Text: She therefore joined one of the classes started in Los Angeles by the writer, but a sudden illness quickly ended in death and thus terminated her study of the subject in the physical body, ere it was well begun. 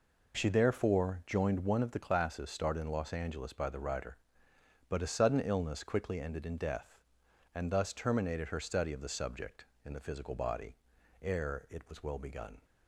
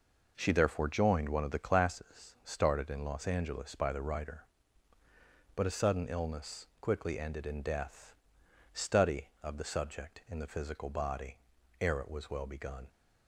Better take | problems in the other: first | skips "and thus terminated her"; at 8.4 s

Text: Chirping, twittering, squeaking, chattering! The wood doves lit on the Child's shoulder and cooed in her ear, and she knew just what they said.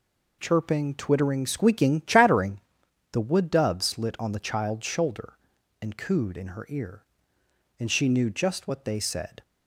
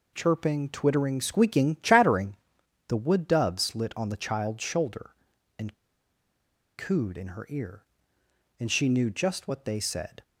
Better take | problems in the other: first | pauses between "and" and "cooed"; at 5.7 s; 1.0 s long

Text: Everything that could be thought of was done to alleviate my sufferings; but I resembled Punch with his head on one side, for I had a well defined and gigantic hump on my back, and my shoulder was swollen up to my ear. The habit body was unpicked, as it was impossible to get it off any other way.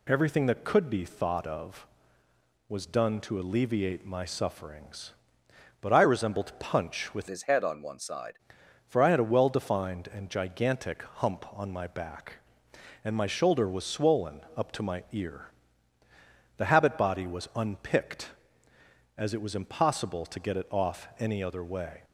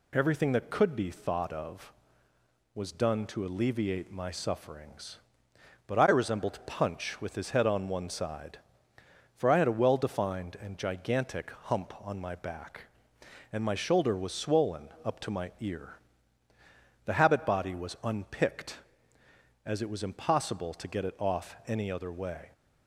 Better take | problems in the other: second | changes voice from "his" to "side"; from 7.2 to 8.3 s; 1.1 s long // pauses between "swollen" and "up"; slight; at 14.3 s; 0.16 s long; slight in the second

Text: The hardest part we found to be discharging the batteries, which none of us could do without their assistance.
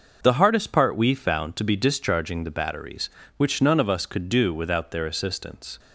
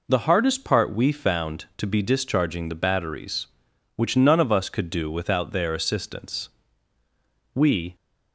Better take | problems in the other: first | goes on to say "We"; slight; from 7.5 s on; 0.40 s long

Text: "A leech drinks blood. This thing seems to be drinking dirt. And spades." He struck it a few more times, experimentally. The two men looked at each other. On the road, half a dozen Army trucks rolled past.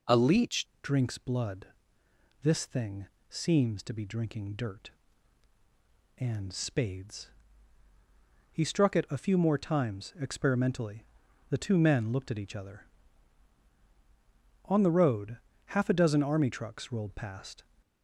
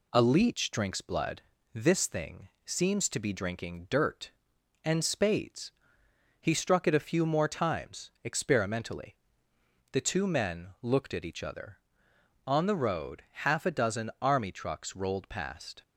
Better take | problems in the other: second | changes voice at "drinks"; from 0.8 s on; 16.8 s long // pauses between "thing" and "seems"; slight; at 3.0 s; 0.22 s long; slight in the second

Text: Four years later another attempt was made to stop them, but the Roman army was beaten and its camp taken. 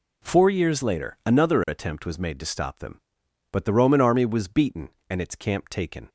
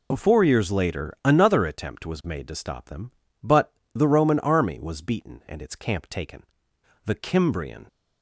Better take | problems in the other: first | pauses between "but" and "the"; slight; at 3.7 s; 0.22 s long // goes on to say "The Cimbrian"; noticeable; from 7.0 s on; 0.82 s long

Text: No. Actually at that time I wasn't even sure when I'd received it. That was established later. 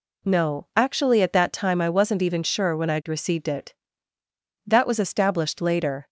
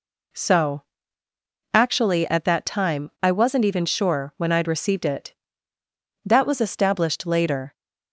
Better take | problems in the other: first | says "So" for "No"; at 0.3 s

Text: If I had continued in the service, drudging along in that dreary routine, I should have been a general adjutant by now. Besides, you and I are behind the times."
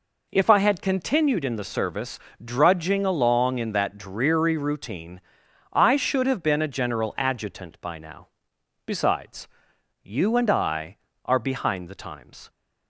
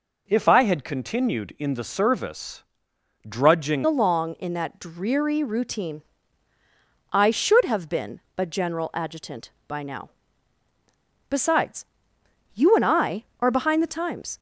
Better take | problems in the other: first | changes voice at "along"; from 3.8 s on; 10.5 s long // pauses between "been" and "a"; slight; at 8.1 s; 0.18 s long

